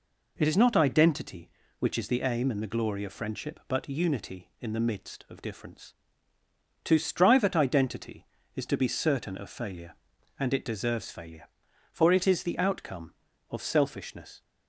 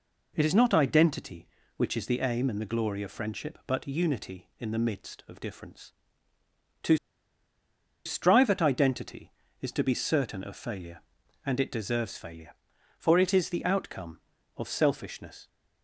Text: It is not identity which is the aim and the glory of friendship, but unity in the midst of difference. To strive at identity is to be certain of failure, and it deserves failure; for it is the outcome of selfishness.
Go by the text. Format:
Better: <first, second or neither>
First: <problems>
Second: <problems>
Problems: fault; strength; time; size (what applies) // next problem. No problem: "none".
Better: first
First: none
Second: pauses between "To" and "strive"; at 6.9 s; 1.0 s long